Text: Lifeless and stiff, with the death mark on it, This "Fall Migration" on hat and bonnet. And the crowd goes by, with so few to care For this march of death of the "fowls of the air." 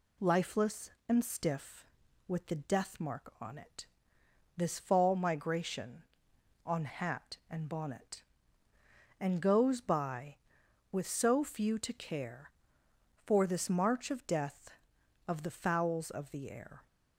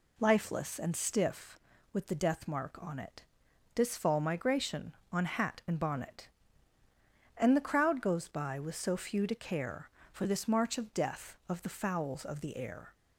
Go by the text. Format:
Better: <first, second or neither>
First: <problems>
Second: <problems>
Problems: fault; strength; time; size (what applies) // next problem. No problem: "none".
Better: second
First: skips "the crowd"; at 9.4 s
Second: none